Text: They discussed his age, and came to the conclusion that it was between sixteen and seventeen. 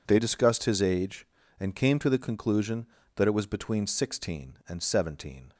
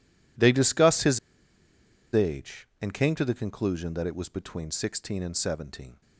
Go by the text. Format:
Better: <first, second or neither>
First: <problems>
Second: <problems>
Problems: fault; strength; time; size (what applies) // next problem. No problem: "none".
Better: first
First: none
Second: pauses between "his" and "age"; noticeable; at 1.1 s; 0.94 s long